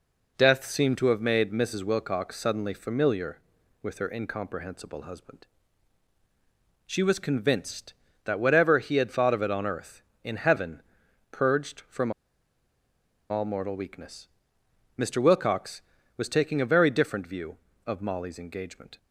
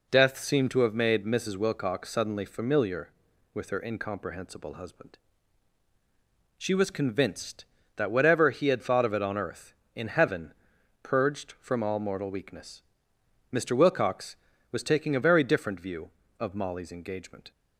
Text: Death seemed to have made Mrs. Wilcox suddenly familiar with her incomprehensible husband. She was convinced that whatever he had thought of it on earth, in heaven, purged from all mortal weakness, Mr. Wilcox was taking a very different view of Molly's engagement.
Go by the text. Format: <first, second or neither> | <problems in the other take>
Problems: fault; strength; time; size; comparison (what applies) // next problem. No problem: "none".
second | pauses between "from" and "all"; at 12.1 s; 1.1 s long